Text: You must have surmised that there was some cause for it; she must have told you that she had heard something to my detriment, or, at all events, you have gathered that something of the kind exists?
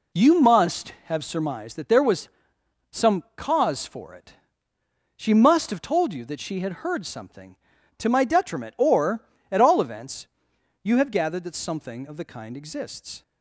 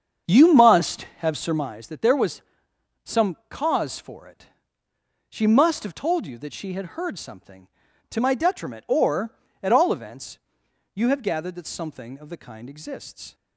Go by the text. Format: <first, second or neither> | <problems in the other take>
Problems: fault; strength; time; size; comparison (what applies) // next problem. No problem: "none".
first | starts louder than the rest; strong; until 1.8 s; 7.5 dB // pauses between "was" and "some"; noticeable; at 2.4 s; 0.62 s long; noticeable in the first